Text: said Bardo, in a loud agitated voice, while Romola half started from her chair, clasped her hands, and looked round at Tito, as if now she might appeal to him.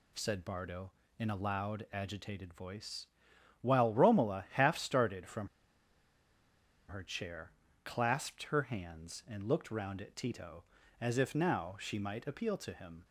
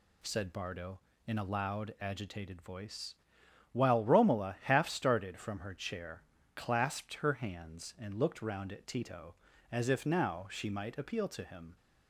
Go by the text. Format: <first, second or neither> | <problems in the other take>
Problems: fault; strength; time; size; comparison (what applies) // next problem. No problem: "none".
second | pauses between "from" and "her"; strong; at 5.4 s; 1.4 s long